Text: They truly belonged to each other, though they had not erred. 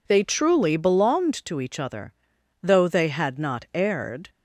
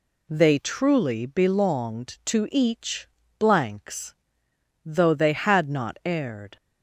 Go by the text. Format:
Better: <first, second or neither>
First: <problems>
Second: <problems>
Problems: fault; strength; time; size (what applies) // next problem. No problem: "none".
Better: first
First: none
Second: says "blanks" for "other"; at 3.3 s